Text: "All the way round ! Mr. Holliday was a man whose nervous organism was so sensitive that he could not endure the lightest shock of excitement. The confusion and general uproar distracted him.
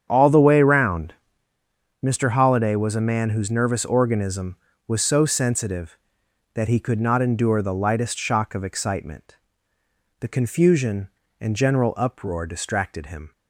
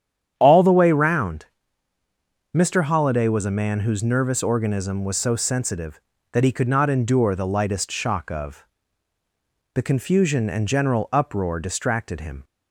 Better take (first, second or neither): first